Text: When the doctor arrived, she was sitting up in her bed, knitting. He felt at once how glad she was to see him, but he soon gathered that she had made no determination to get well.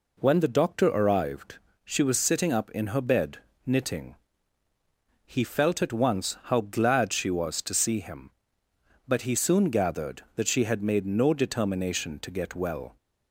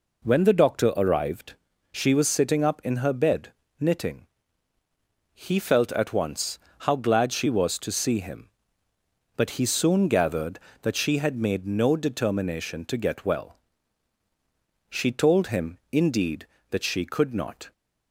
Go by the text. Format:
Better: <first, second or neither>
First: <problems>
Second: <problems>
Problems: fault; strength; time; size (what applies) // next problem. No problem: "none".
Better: first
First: none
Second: pauses between "once" and "how"; slight; at 6.6 s; 0.20 s long // goes on to say "She told him indeed that she could not"; strong; from 14.9 s on; 2.8 s long